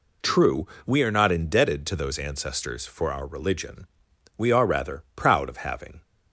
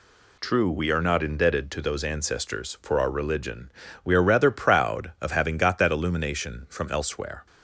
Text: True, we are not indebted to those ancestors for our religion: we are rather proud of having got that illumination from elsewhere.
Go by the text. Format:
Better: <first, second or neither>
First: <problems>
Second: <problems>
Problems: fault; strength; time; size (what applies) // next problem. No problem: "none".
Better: second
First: stops before "got that illumination from elsewhere"; at 6.0 s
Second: none